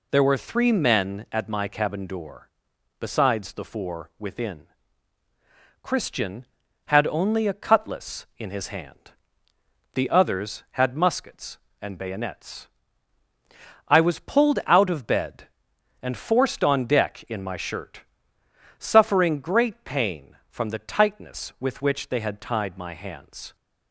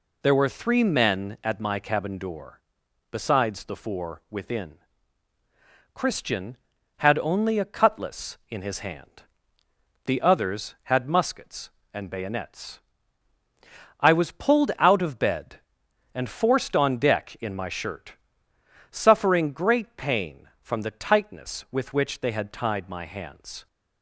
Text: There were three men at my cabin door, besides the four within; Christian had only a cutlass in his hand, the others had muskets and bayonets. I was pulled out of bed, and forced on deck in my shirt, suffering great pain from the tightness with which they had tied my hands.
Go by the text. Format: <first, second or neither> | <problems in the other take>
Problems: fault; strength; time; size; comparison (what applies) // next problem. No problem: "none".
neither | none